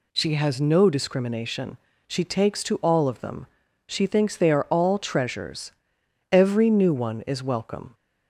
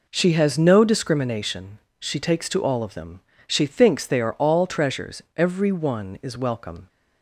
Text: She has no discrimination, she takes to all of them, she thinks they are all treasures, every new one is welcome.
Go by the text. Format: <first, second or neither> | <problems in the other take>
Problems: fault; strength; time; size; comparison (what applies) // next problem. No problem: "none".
first | skips "new"; at 5.7 s